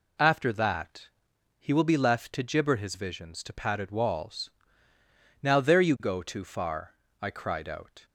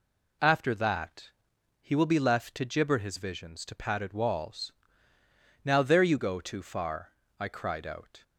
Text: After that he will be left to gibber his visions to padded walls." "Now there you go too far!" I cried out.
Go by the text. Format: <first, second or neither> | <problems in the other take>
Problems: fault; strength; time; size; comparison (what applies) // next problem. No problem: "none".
neither | pauses between "that" and "he"; noticeable; the same in both